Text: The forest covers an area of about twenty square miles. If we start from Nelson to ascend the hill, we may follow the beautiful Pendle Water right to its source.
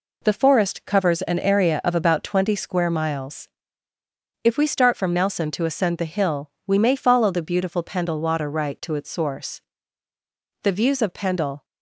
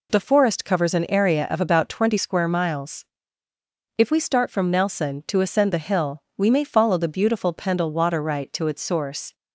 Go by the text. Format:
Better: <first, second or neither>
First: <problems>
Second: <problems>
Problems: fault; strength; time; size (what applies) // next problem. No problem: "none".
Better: second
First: goes on to say "The views of Pendle"; noticeable; from 10.6 s on; 1.0 s long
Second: none